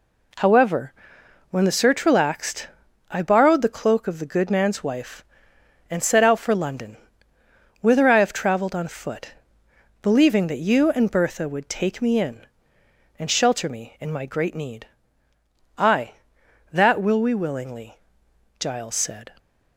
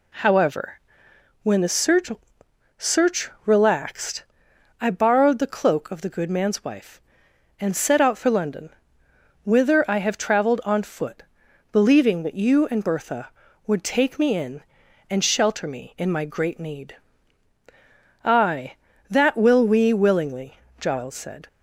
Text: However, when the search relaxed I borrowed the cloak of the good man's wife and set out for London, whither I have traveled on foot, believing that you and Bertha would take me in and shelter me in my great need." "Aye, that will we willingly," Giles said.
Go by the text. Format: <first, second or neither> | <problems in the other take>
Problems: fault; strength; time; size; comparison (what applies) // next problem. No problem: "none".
first | says "search" twice; at 2.7 s // pauses between "relaxed" and "I"; noticeable; at 4.2 s; 0.56 s long; noticeable in the first